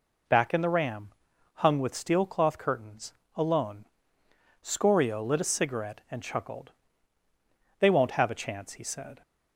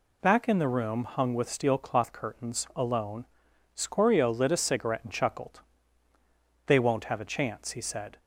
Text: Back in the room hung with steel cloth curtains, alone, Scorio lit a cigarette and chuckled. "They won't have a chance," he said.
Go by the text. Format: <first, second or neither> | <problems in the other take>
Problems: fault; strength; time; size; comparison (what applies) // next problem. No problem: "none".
second | says "ram" for "room"; at 0.6 s